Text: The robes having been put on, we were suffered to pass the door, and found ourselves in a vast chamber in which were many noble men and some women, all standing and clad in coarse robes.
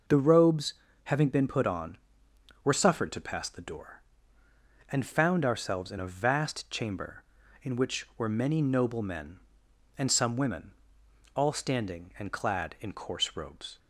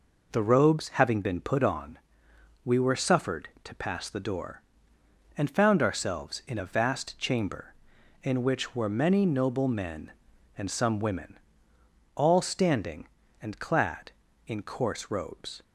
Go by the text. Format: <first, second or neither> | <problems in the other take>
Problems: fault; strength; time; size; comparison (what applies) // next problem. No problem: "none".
second | pauses between "robes" and "having"; slight; at 0.7 s; 0.30 s long // skips "we"; at 2.2 s